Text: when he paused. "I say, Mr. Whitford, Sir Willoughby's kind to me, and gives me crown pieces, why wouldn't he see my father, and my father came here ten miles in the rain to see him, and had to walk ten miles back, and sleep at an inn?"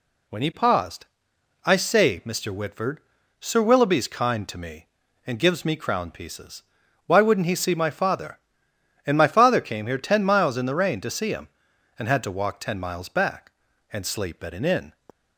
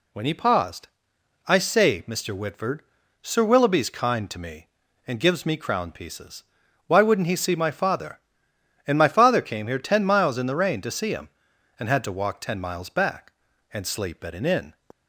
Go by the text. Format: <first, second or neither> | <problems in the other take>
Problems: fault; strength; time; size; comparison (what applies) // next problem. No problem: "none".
neither | none